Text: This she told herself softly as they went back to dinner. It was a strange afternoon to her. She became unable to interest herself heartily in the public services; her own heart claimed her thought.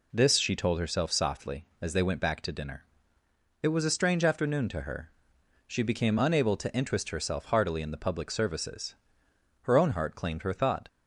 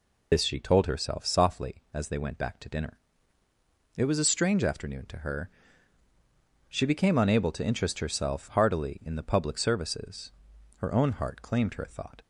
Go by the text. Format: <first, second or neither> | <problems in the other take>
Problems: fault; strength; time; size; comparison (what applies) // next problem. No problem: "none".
first | loses the start of "This"; at 0.3 s; 75 ms